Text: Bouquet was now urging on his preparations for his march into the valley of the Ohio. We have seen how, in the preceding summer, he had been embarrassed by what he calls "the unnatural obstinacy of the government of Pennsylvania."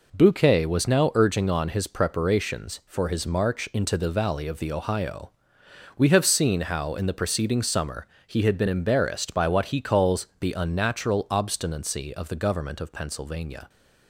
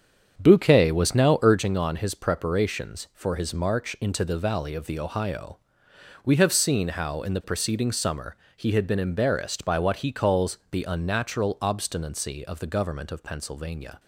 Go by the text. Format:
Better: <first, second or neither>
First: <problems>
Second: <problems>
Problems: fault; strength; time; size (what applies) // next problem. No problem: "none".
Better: first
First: none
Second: starts louder than the rest; strong; until 1.6 s; 7.5 dB